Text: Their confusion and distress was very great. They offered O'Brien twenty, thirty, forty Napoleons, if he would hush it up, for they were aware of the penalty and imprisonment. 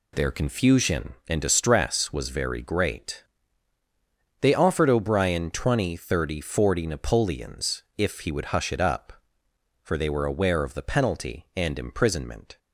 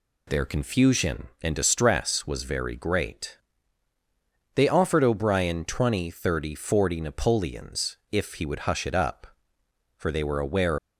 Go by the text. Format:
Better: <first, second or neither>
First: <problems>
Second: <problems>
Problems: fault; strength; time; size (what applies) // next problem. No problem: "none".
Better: first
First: none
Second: stops before "of the penalty and imprisonment"; at 10.7 s